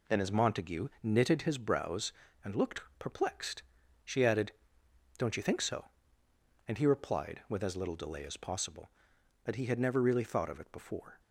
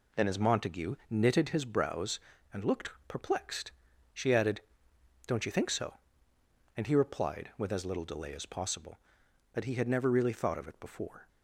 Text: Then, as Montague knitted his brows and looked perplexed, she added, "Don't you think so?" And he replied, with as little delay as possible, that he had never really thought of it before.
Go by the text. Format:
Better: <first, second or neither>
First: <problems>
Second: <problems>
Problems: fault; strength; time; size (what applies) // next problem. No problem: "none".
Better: neither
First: pauses between "looked" and "perplexed"; slight; at 2.8 s; 0.18 s long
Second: pauses between "looked" and "perplexed"; slight; at 2.9 s; 0.18 s long